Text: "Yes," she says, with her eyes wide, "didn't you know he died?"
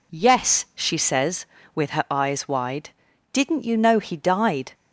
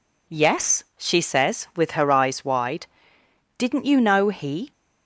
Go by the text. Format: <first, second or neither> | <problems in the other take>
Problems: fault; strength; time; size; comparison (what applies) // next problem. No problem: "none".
first | stops before "died"; at 4.7 s